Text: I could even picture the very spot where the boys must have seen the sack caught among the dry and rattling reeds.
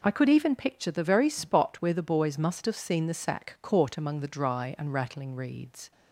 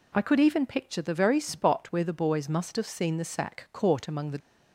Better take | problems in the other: first | stops before "dry and rattling reeds"; at 4.3 s

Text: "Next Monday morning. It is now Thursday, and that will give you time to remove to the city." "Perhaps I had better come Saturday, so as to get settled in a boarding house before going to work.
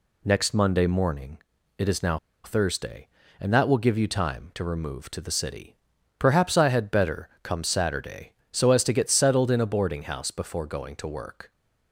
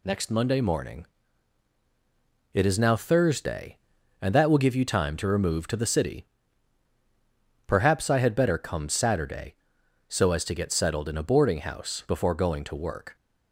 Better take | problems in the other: second | pauses between "now" and "Thursday"; slight; at 2.1 s; 0.27 s long

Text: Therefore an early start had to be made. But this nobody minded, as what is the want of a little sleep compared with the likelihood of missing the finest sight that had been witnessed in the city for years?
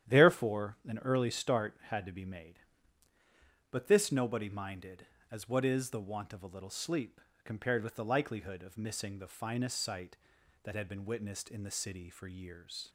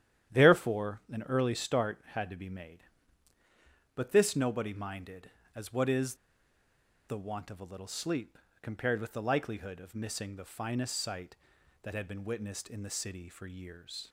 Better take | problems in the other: first | starts louder than the rest; strong; until 1.4 s; 10.5 dB; strong in the first // pauses between "is" and "the"; noticeable; at 6.1 s; 0.93 s long // pauses between "sleep" and "compared"; slight; at 8.3 s; 0.22 s long; slight in the first

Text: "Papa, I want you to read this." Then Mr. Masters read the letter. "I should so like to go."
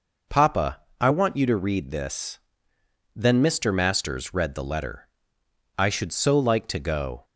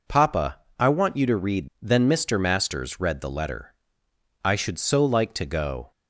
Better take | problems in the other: first | skips "this"; at 1.7 s

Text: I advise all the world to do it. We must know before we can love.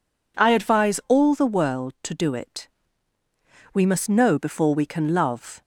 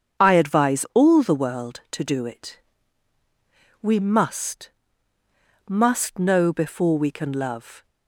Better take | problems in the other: first | starts louder than the rest; strong; until 1.2 s; 7 dB // says "must" twice; at 5.6 s

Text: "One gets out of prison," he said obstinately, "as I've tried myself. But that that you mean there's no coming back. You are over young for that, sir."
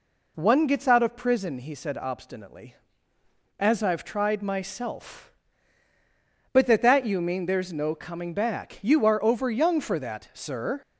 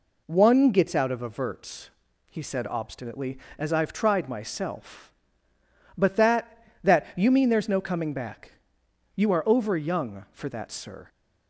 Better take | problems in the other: first | says "averts" for "prison"; at 1.2 s

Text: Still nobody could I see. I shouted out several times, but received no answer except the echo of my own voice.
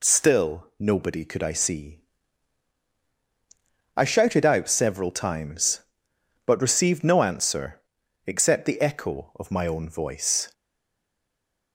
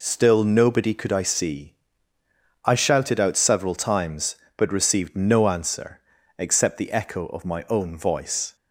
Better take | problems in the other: second | pauses between "answer" and "except"; noticeable; at 7.8 s; 0.46 s long; also in the second // stays silent after the last word; noticeable; from 10.5 s on; 1.2 s long

